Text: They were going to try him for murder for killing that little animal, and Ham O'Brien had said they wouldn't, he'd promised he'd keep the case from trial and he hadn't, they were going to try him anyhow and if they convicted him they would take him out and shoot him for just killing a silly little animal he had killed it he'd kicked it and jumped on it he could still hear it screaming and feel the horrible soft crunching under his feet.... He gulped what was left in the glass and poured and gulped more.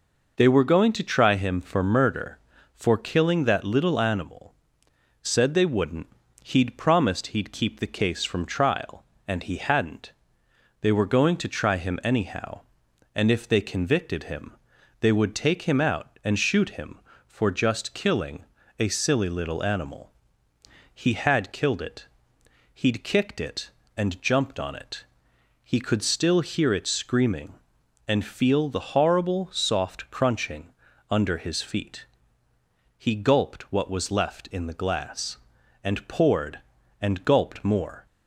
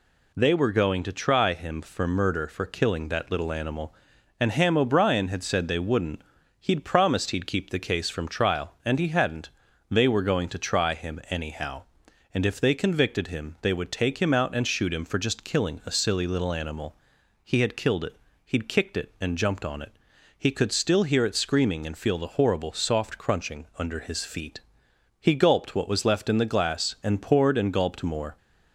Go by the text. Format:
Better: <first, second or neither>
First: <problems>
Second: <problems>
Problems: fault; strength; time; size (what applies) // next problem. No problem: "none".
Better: second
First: skips "and Ham O'Brien had"; at 4.8 s // pauses between "him" and "they"; noticeable; at 14.5 s; 0.46 s long // pauses between "killing" and "a"; slight; at 18.4 s; 0.36 s long // pauses between "animal" and "he"; noticeable; at 20.0 s; 0.84 s long // pauses between "it" and "he'd"; noticeable; at 22.0 s; 0.68 s long // pauses between "it" and "he"; noticeable; at 25.0 s; 0.58 s long // pauses between "crunching" and "under"; at 30.6 s; 0.40 s long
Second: pauses between "animal" and "he"; noticeable; at 16.9 s; 0.48 s long // pauses between "it" and "he'd"; slight; at 18.1 s; 0.30 s long // pauses between "it" and "he"; at 19.9 s; 0.40 s long